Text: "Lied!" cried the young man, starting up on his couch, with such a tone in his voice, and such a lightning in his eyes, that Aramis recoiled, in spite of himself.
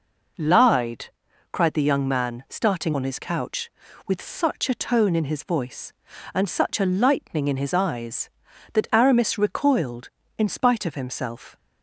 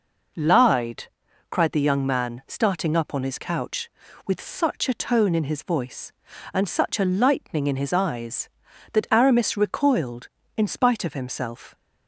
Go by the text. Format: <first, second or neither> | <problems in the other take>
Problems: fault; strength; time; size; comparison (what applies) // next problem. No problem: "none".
second | skips "up"; at 2.9 s